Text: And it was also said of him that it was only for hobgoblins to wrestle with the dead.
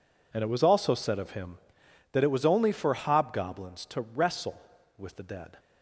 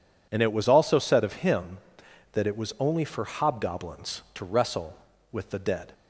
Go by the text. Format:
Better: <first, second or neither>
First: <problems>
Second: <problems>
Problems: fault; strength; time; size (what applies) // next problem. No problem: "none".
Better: neither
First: none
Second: none